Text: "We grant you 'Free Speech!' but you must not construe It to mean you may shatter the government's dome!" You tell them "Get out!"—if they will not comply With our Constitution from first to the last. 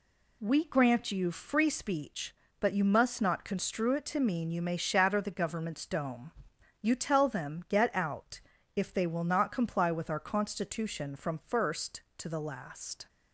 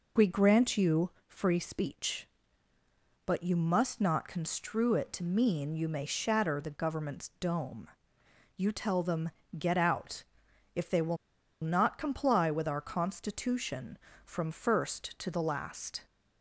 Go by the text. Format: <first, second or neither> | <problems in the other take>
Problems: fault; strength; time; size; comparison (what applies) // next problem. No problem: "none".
first | pauses between "you" and "Free"; slight; at 1.1 s; 0.16 s long // pauses between "them" and "Get"; slight; at 9.2 s; 0.30 s long // pauses between "will" and "not"; noticeable; at 11.1 s; 0.46 s long